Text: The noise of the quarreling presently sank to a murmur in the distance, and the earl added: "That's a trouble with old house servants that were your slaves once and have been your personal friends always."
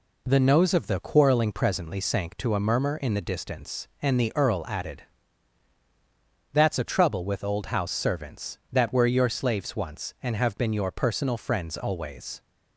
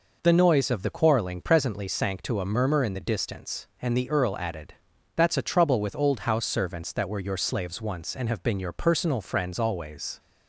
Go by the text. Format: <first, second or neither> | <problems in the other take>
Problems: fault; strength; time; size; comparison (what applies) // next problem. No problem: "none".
second | says "nose" for "noise"; at 0.4 s